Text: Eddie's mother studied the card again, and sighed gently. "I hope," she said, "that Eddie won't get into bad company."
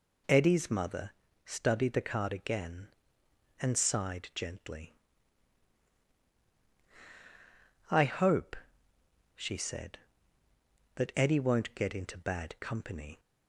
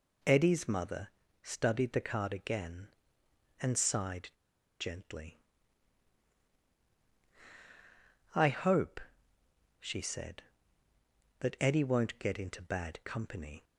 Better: first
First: pauses between "mother" and "studied"; slight; at 1.1 s; 0.34 s long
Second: pauses between "mother" and "studied"; slight; at 1.0 s; 0.34 s long // pauses between "sighed" and "gently"; noticeable; at 4.2 s; 0.50 s long

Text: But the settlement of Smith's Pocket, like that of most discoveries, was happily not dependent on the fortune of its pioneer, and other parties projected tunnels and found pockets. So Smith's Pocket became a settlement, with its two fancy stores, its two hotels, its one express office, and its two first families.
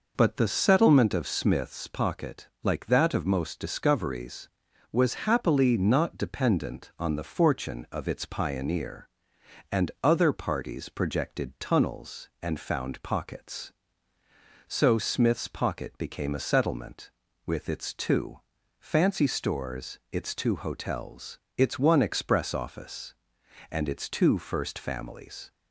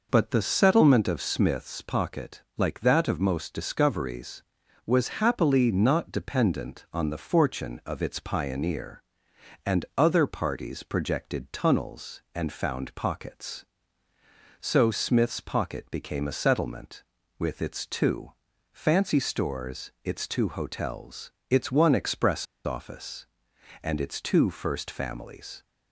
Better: first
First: pauses between "two" and "fancy"; at 18.3 s; 0.40 s long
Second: pauses between "two" and "fancy"; at 18.3 s; 0.40 s long // pauses between "express" and "office"; slight; at 22.4 s; 0.22 s long

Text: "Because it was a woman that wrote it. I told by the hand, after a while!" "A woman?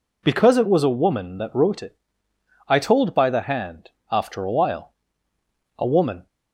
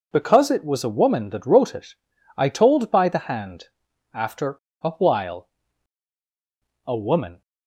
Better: first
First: none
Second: pauses between "after" and "a"; slight; at 4.5 s; 0.25 s long

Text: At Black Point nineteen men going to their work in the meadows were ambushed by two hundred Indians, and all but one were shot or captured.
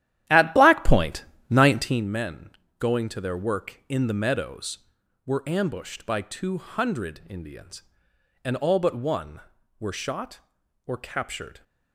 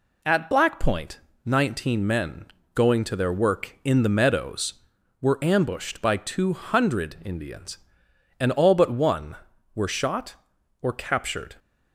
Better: second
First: starts louder than the rest; strong; until 2.1 s; 12 dB // pauses between "Point" and "nineteen"; slight; at 1.2 s; 0.24 s long // pauses between "men" and "going"; slight; at 2.5 s; 0.28 s long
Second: pauses between "Point" and "nineteen"; slight; at 1.2 s; 0.24 s long // pauses between "men" and "going"; slight; at 2.4 s; 0.28 s long

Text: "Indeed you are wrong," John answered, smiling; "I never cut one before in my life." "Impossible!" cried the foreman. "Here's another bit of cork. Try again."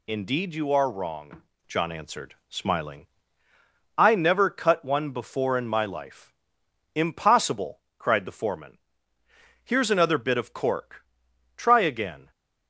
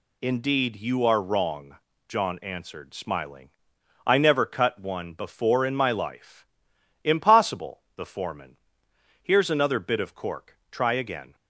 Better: first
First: none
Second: skips "cried"; at 7.8 s

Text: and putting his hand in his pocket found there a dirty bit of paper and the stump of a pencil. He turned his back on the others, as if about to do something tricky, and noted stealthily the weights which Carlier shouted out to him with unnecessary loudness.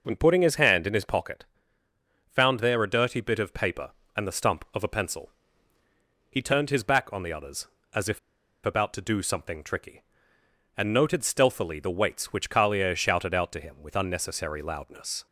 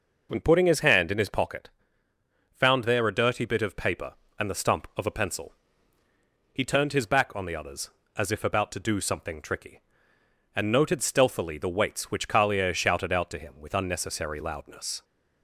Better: second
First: pauses between "pocket" and "found"; noticeable; at 1.4 s; 0.86 s long // pauses between "if" and "about"; at 8.1 s; 0.45 s long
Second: pauses between "pocket" and "found"; noticeable; at 1.6 s; 0.86 s long

